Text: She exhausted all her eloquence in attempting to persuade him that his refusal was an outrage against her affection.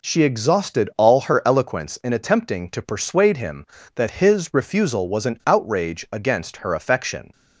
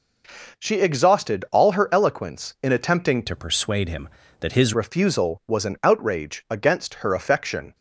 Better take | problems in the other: first | changes voice from "to" to "his"; from 3.2 to 4.7 s; 1.5 s long

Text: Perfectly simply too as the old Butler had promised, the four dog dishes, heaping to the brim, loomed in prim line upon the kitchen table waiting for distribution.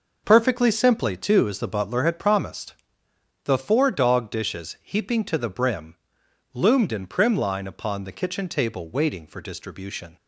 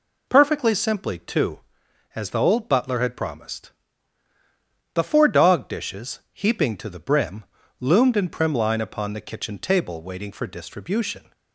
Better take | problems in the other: second | skips "old"; at 1.6 s

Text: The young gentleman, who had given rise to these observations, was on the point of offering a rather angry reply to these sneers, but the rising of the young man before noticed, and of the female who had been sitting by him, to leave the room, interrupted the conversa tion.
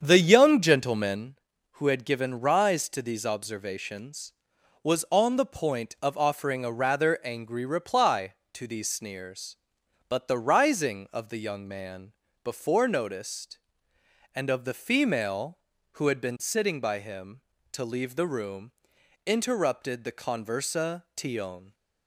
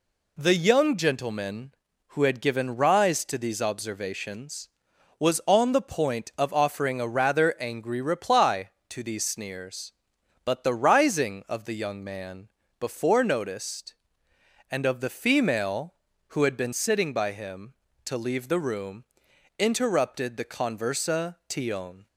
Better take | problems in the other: second | starts louder than the rest; strong; until 1.2 s; 8 dB // pauses between "man" and "before"; slight; at 12.1 s; 0.28 s long; slight in the second

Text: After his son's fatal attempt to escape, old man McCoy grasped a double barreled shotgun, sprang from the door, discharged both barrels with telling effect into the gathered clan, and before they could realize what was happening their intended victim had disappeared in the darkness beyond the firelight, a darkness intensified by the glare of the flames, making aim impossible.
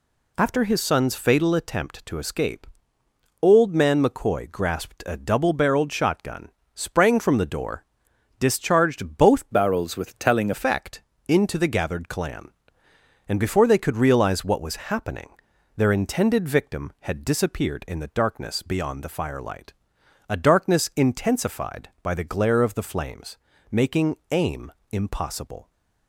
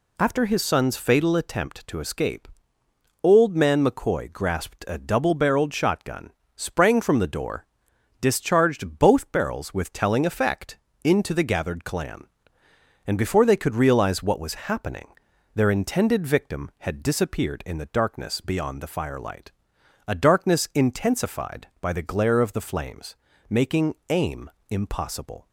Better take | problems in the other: second | changes voice from "barrels" to "telling"; from 9.5 to 10.5 s; 1.0 s long // pauses between "effect" and "into"; slight; at 11.0 s; 0.26 s long; slight in the second // pauses between "happening" and "their"; noticeable; at 15.2 s; 0.46 s long; noticeable in the second // pauses between "making" and "aim"; slight; at 24.1 s; 0.16 s long; slight in the second // pauses between "aim" and "impossible"; slight; at 24.7 s; 0.18 s long; slight in the second

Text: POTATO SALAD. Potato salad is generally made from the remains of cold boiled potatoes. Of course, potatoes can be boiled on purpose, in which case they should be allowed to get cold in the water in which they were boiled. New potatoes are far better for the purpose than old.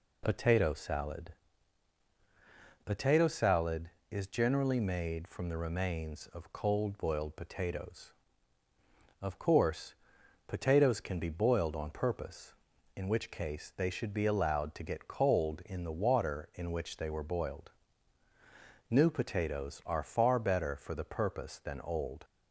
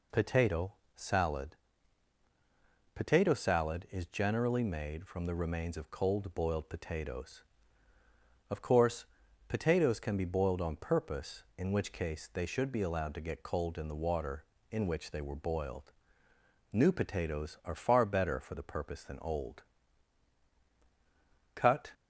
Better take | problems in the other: first | pauses between "POTATO" and "SALAD"; slight; at 0.7 s; 0.24 s long // goes on to say "Cut"; slight; from 21.5 s on; 0.38 s long

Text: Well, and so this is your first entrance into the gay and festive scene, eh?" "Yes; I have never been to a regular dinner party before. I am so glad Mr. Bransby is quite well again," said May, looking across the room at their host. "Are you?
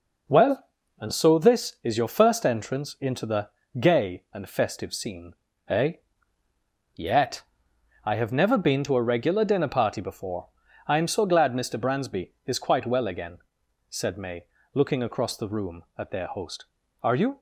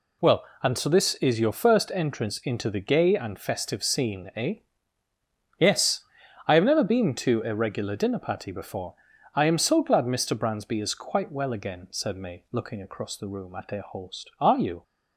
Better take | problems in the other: second | pauses between "the" and "gay"; slight; at 3.4 s; 0.30 s long // says "Yet" for "Yes"; at 6.9 s

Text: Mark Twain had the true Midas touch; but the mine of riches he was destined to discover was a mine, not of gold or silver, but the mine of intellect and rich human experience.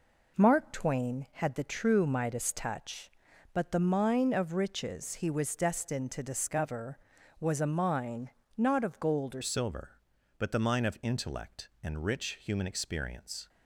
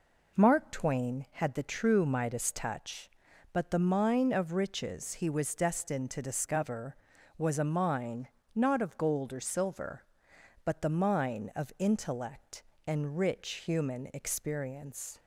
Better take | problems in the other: second | changes voice at "silver"; from 9.4 s on; 4.0 s long

